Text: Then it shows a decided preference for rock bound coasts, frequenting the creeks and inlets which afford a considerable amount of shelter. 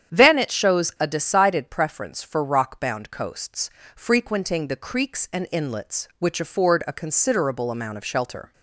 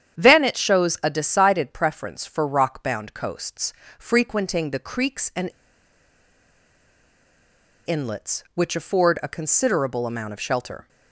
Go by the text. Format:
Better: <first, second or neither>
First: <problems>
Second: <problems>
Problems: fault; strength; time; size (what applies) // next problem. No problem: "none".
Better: first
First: starts louder than the rest; strong; until 1.2 s; 9 dB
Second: starts louder than the rest; strong; until 1.2 s; 9 dB // pauses between "and" and "inlets"; strong; at 5.5 s; 2.3 s long